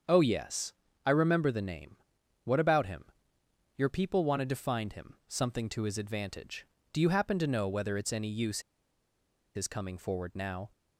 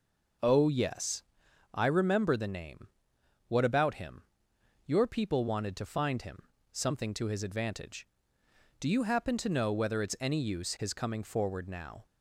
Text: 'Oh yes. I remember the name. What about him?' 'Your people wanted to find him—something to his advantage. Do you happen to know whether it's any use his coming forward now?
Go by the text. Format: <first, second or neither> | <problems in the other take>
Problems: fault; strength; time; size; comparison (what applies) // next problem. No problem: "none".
second | starts louder than the rest; strong; until 1.3 s; 7 dB // pauses between "use" and "his"; noticeable; at 8.6 s; 0.95 s long